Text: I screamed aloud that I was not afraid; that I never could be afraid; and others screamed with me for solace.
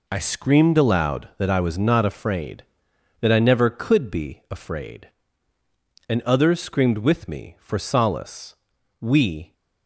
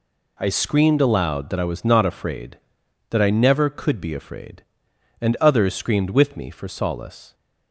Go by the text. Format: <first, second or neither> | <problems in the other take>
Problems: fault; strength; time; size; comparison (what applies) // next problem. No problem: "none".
second | goes on to say "We"; from 9.0 s on; 0.52 s long